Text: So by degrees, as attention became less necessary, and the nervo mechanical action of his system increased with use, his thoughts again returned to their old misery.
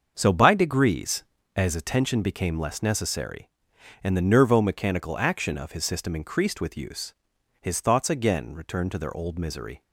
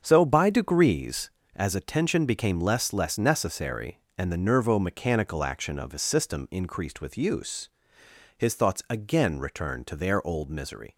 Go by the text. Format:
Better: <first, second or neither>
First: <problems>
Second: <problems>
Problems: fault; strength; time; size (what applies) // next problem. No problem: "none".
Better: first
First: starts louder than the rest; until 1.1 s; 6.5 dB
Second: starts louder than the rest; strong; until 1.0 s; 7 dB // says "less" twice; at 2.9 s